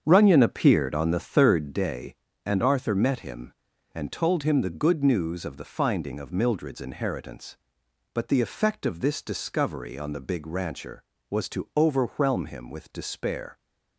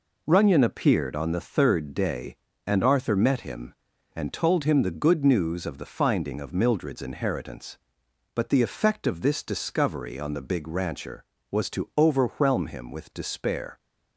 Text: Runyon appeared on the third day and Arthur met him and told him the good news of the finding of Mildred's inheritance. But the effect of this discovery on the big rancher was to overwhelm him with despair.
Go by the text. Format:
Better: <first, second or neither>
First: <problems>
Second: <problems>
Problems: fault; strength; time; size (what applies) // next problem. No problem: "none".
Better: second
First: starts louder than the rest; strong; until 1.8 s; 7.5 dB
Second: none